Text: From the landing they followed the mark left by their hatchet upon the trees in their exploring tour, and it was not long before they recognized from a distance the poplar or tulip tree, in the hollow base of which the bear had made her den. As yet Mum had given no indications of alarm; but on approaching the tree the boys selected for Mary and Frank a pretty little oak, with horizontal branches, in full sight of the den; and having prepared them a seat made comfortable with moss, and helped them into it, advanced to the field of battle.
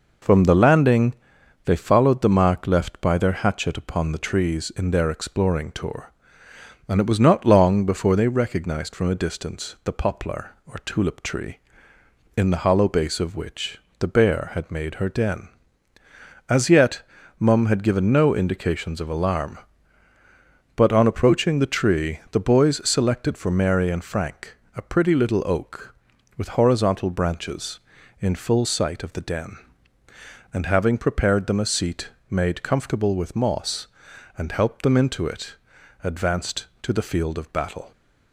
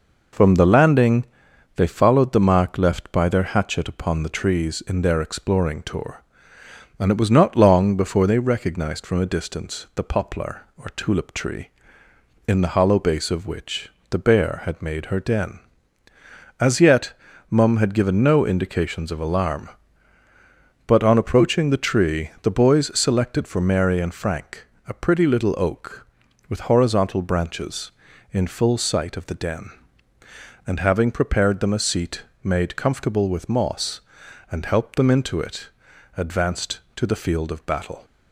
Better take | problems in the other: neither | pauses between "landing" and "they"; noticeable; the same in both // pauses between "which" and "the"; slight; the same in both // pauses between "yet" and "Mum"; slight; the same in both // pauses between "Frank" and "a"; slight; the same in both // pauses between "seat" and "made"; slight; the same in both

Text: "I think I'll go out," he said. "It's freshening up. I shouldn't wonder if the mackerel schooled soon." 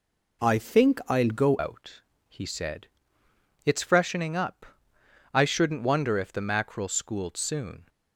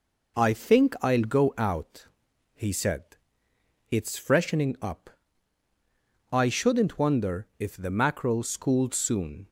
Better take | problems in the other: second | changes voice at "out"; from 1.5 s on; 6.3 s long

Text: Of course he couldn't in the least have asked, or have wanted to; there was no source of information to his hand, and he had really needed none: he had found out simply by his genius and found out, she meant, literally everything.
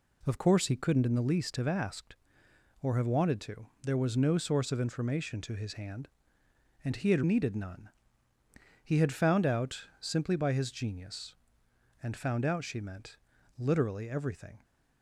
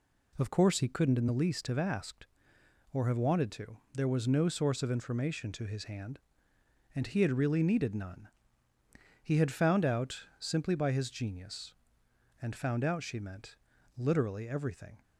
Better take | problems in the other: second | skips "really"; at 7.2 s

